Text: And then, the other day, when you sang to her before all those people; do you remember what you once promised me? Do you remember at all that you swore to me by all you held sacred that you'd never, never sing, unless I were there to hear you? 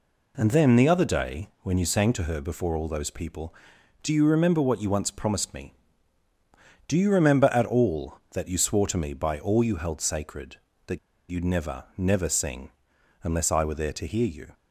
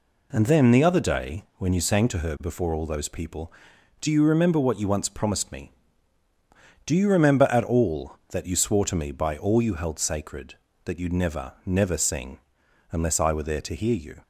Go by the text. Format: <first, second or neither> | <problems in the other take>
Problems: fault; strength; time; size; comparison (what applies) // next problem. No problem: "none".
second | pauses between "that" and "you'd"; slight; at 10.9 s; 0.30 s long